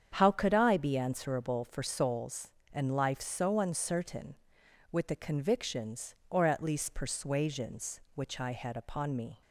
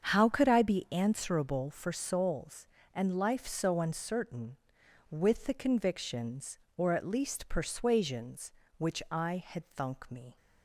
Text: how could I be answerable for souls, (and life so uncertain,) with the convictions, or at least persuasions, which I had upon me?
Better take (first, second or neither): first